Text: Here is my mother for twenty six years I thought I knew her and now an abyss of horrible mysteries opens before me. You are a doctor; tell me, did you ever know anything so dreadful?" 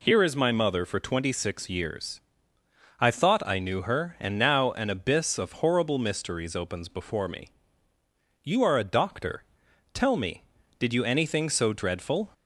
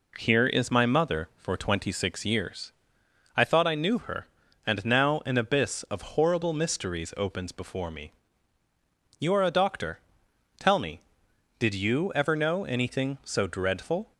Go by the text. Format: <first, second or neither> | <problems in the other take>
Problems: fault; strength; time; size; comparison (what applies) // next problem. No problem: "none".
second | pauses between "years" and "I"; noticeable; at 2.2 s; 0.78 s long; noticeable in the second // skips "ever know"; at 11.0 s